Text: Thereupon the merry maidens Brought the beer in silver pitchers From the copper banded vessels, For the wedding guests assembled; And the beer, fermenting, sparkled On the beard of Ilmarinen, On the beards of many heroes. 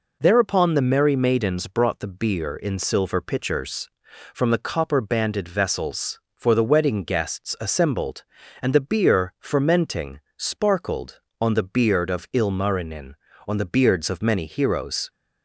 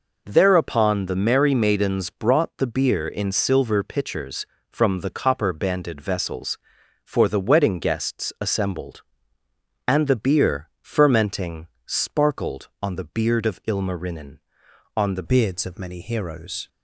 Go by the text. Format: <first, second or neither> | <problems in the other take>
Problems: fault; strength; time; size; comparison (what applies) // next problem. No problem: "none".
first | changes voice at "beards"; from 15.2 s on; 1.4 s long